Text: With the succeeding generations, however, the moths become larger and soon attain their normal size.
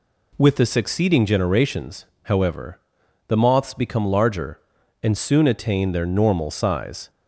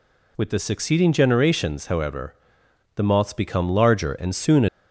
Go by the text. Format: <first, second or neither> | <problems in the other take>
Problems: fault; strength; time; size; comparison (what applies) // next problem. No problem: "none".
first | stops before "attain their normal size"; at 4.6 s